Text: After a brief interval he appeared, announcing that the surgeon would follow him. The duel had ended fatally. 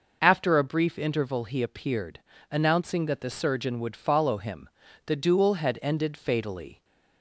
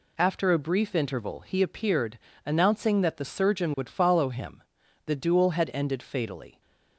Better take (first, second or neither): neither